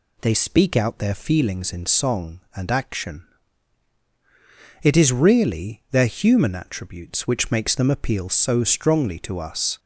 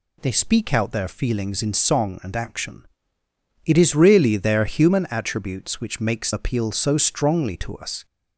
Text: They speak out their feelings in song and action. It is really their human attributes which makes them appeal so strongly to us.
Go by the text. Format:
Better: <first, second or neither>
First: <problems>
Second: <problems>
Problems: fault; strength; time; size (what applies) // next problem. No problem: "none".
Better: first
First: none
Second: skips "them"; at 6.3 s